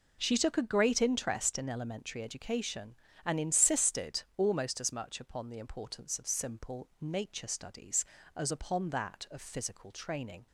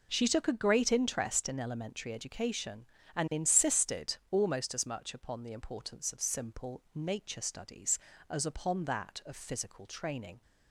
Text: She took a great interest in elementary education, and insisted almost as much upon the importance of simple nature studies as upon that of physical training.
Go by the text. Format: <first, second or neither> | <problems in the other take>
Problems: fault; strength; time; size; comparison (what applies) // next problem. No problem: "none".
neither | none